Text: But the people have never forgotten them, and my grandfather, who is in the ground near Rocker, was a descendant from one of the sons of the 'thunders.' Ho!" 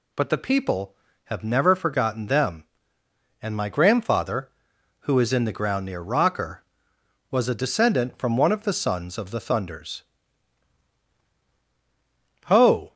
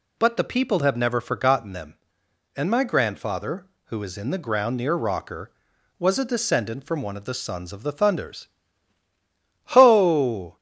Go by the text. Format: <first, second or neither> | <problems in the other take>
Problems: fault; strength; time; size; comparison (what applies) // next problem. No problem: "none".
neither | none